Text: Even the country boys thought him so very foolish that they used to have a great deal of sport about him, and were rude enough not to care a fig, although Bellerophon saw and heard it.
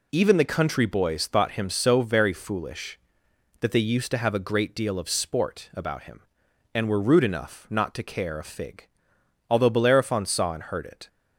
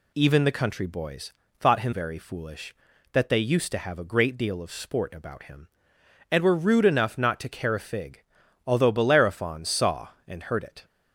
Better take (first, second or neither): first